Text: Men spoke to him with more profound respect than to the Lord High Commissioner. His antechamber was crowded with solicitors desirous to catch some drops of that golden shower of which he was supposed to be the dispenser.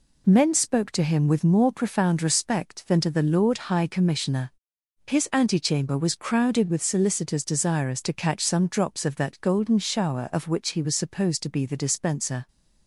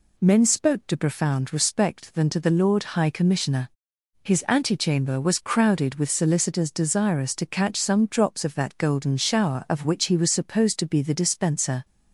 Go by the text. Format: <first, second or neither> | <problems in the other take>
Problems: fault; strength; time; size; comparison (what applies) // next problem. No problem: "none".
first | skips "him with more"; at 0.9 s